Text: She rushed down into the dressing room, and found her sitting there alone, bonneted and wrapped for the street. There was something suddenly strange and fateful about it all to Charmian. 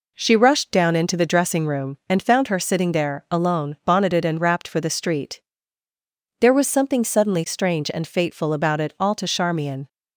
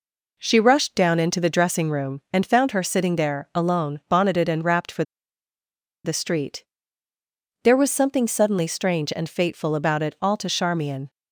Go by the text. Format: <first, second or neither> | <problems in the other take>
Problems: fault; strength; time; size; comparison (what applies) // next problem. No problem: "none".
first | pauses between "for" and "the"; at 5.0 s; 1.0 s long